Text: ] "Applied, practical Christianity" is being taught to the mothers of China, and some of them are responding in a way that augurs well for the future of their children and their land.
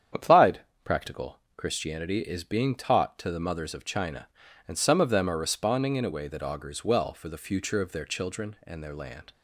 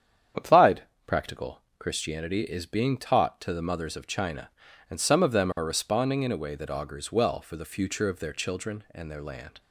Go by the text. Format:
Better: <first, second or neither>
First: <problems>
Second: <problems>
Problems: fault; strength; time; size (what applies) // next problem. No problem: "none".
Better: neither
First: starts louder than the rest; strong; until 1.4 s; 8.5 dB // pauses between "practical" and "Christianity"; slight; at 1.3 s; 0.16 s long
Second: starts louder than the rest; strong; until 1.6 s; 8.5 dB // pauses between "practical" and "Christianity"; slight; at 1.6 s; 0.16 s long